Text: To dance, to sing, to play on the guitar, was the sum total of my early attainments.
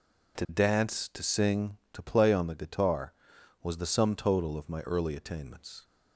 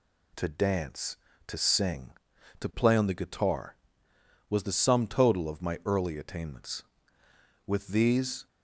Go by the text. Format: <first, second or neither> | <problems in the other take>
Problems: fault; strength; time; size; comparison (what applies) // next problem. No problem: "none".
first | goes on to say "With these"; noticeable; from 7.6 s on; 0.80 s long